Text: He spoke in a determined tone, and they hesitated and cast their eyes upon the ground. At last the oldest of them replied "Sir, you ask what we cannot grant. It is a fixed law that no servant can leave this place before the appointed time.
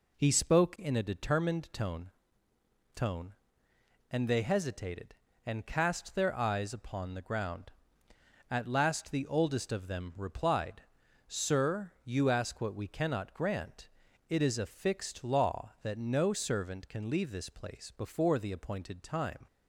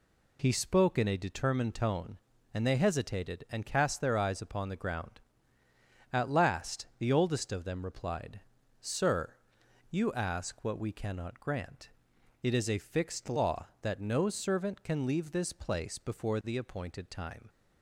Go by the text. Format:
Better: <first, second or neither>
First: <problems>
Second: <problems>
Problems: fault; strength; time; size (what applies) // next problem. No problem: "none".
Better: second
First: says "tone" twice; at 2.9 s // pauses between "replied" and "Sir"; noticeable; at 10.8 s; 0.48 s long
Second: pauses between "replied" and "Sir"; at 8.4 s; 0.40 s long